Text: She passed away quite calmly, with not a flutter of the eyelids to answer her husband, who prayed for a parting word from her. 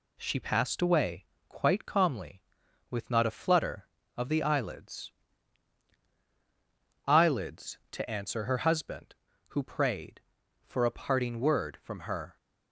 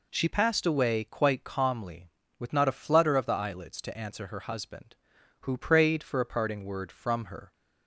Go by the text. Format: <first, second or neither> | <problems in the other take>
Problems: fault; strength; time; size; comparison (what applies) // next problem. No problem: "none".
second | pauses between "away" and "quite"; slight; at 1.2 s; 0.22 s long // says "eyelids" twice; at 7.0 s